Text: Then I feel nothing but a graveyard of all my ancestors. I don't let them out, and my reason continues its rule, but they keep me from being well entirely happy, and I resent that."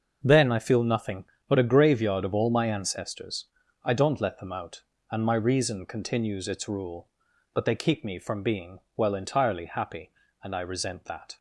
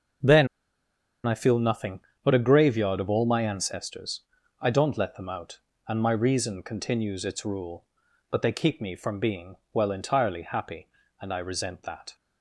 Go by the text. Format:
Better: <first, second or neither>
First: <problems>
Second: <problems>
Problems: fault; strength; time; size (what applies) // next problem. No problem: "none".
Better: first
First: starts louder than the rest; until 1.2 s; 6 dB // pauses between "being" and "well"; slight; at 8.8 s; 0.18 s long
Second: starts louder than the rest; noticeable; until 2.2 s; 6 dB // pauses between "Then" and "I"; noticeable; at 0.4 s; 0.79 s long // pauses between "being" and "well"; slight; at 9.5 s; 0.18 s long